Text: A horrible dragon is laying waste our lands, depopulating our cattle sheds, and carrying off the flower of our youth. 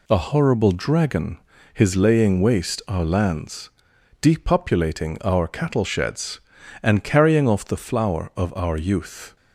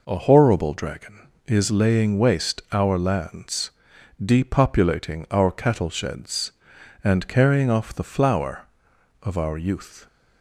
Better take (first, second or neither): second